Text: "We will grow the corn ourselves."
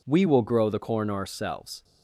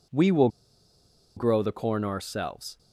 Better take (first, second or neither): first